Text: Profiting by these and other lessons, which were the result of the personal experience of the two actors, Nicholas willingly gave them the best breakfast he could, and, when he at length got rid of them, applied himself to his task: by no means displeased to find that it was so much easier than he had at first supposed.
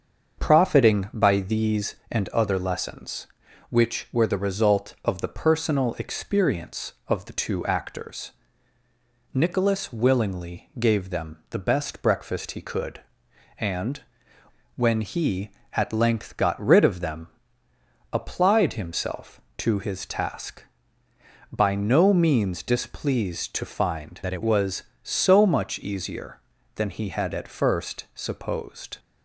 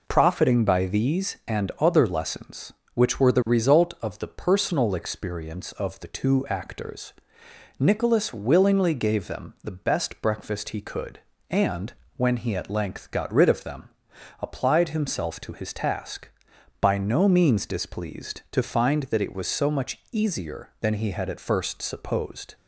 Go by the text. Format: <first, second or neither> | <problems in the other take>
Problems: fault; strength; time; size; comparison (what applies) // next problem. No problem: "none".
second | starts louder than the rest; until 1.4 s; 6.5 dB // changes voice from "that" to "it"; from 24.2 to 24.4 s; 0.2 s long